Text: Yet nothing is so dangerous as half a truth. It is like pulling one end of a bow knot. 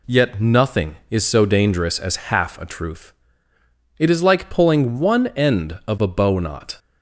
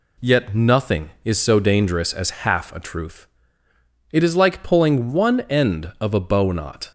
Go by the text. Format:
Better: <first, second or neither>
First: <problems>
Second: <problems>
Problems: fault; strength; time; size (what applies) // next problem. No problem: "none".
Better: neither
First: none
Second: none